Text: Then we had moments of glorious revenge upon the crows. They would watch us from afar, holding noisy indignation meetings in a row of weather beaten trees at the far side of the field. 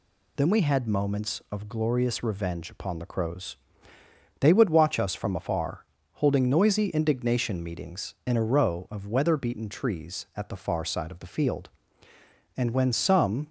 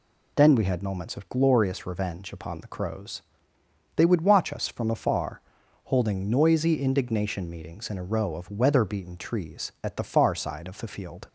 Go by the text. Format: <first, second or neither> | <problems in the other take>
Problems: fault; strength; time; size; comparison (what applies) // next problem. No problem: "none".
second | goes on to say "And when some"; noticeable; from 12.5 s on; 0.90 s long